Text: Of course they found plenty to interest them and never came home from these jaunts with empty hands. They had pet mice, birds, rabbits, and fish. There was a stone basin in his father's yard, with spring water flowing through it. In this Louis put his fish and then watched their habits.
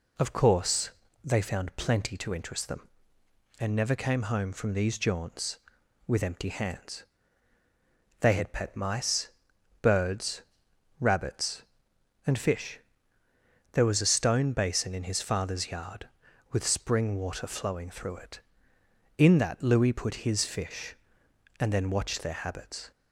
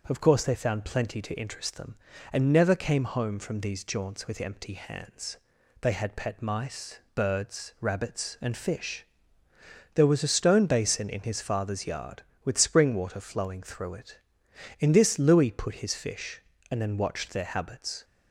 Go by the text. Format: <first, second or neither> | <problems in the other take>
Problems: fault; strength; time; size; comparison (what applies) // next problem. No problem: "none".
second | pauses between "course" and "they"; slight; at 0.9 s; 0.30 s long // says "that" for "this"; at 19.3 s